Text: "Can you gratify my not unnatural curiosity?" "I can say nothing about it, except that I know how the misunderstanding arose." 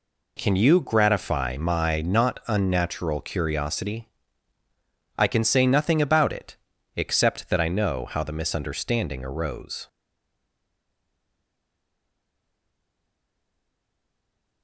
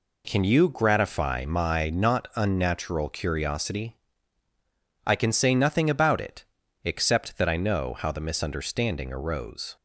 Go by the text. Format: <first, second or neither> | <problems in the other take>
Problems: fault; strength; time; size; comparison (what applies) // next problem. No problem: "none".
second | stays silent after the last word; strong; from 9.8 s on; 4.8 s long